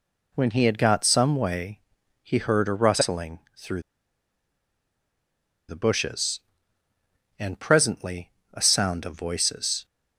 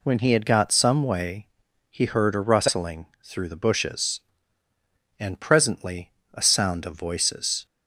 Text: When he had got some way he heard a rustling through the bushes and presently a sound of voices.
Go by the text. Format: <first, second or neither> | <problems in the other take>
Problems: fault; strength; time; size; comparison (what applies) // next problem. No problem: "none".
second | pauses between "way" and "he"; at 1.8 s; 0.42 s long; also in the second // pauses between "rustling" and "through"; slight; at 3.4 s; 0.18 s long; slight in the second // pauses between "through" and "the"; strong; at 3.8 s; 1.8 s long // pauses between "presently" and "a"; slight; at 8.3 s; 0.20 s long; slight in the second